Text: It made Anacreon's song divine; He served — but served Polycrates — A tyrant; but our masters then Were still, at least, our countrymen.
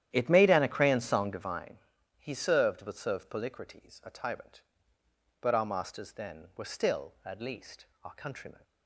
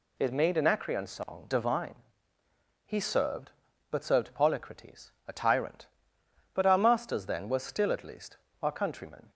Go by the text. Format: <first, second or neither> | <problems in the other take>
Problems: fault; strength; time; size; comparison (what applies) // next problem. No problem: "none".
second | starts louder than the rest; strong; until 1.6 s; 11 dB